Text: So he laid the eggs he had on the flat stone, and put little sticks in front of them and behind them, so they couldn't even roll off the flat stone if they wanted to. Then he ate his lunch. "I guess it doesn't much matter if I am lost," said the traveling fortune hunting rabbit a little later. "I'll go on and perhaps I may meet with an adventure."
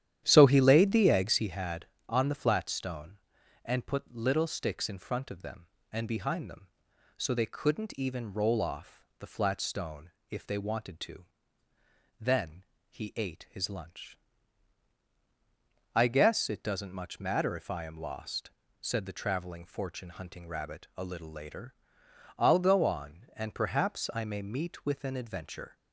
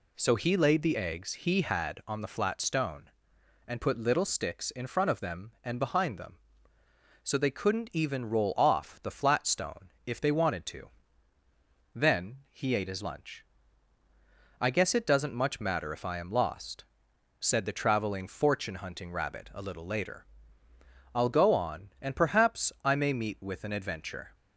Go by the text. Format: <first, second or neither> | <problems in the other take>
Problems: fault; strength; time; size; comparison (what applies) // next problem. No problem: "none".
second | starts louder than the rest; strong; until 1.5 s; 11 dB // pauses between "off" and "the"; slight; at 9.0 s; 0.16 s long // pauses between "stone" and "if"; slight; at 10.0 s; 0.20 s long; slight in the second // pauses between "Then" and "he"; slight; at 12.6 s; 0.26 s long